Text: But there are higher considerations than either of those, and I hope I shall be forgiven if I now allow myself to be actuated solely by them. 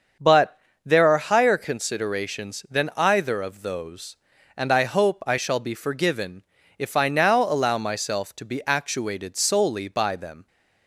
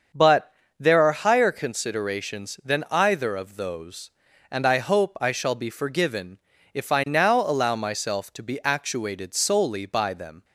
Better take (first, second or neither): neither